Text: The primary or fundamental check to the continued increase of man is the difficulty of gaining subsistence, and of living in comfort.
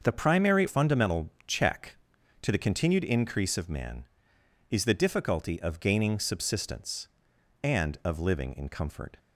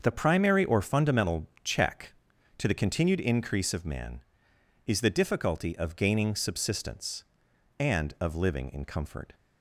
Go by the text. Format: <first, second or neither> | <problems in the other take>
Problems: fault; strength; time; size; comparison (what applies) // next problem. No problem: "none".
second | starts louder than the rest; until 1.0 s; 6.5 dB; also in the second // skips "or"; at 0.6 s // pauses between "fundamental" and "check"; slight; at 1.2 s; 0.18 s long; slight in the second